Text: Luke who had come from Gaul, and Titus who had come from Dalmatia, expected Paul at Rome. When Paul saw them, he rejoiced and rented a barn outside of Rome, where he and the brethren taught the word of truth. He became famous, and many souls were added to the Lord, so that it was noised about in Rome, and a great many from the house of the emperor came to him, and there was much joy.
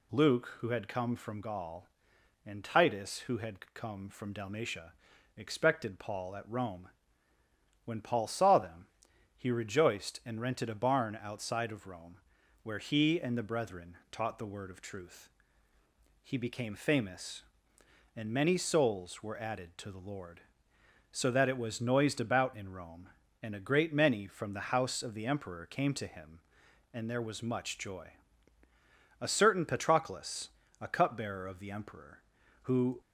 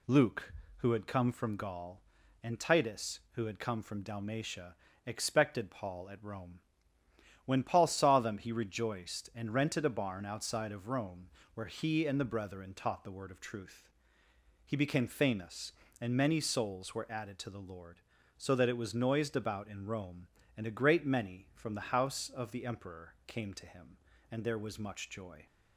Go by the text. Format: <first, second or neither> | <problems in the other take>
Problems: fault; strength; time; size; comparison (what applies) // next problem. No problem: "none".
second | goes on to say "A certain Patroclus a cupbearer of the emperor who"; strong; from 29.2 s on; 3.7 s long